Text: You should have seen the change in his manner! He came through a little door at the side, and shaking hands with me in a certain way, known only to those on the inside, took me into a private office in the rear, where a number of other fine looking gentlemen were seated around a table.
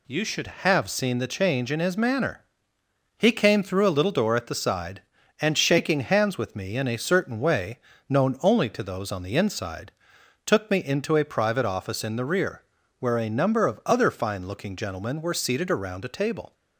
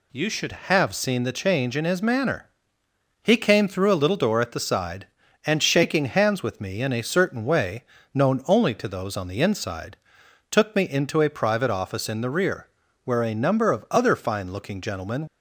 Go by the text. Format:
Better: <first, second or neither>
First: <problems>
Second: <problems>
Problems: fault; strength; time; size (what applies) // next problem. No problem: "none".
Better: first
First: none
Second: stops before "were seated around a table"; at 15.2 s